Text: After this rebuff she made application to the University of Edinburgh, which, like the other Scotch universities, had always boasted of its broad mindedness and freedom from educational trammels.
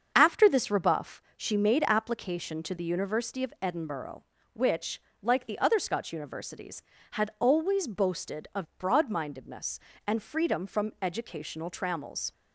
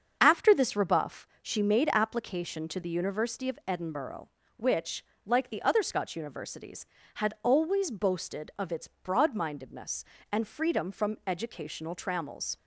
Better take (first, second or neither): second